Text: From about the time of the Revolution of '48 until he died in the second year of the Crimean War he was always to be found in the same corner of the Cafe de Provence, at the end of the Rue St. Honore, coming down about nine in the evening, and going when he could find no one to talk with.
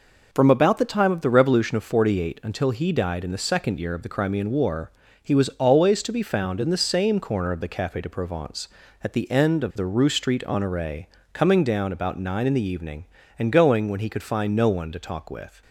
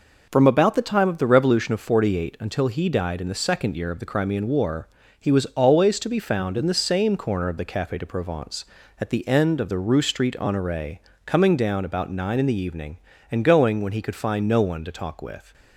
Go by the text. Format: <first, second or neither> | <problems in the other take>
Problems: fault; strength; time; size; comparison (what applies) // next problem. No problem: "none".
neither | pauses between "War" and "he"; slight; the same in both